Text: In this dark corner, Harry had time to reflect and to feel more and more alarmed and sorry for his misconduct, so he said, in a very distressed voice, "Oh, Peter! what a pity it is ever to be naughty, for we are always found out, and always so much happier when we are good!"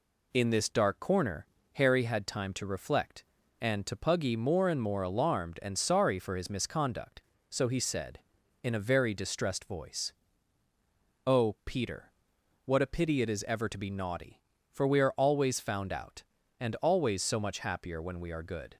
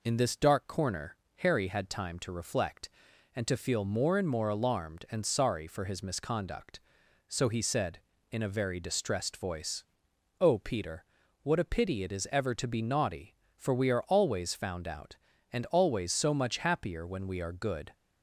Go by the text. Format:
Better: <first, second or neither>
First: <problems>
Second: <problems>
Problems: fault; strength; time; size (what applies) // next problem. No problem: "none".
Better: second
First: says "puggy" for "feel"; at 3.9 s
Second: none